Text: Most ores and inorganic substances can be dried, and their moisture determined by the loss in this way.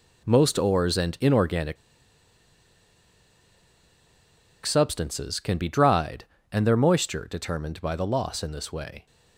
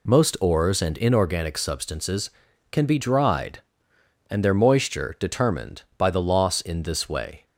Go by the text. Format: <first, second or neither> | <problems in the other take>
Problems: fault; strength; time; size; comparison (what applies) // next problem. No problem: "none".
second | pauses between "inorganic" and "substances"; strong; at 1.7 s; 2.8 s long